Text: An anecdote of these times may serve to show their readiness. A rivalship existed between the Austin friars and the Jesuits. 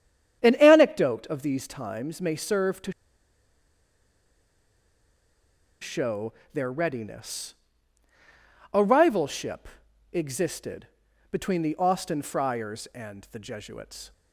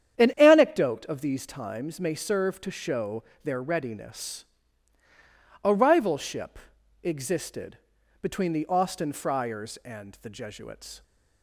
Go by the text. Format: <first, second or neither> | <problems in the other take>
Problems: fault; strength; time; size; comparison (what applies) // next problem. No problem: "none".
second | starts louder than the rest; strong; until 1.4 s; 9 dB; strong in the second // pauses between "to" and "show"; strong; at 2.9 s; 2.8 s long // pauses between "show" and "their"; slight; at 6.3 s; 0.22 s long; slight in the second // pauses between "rivalship" and "existed"; at 9.6 s; 0.44 s long; also in the second // pauses between "existed" and "between"; noticeable; at 10.8 s; 0.46 s long; noticeable in the second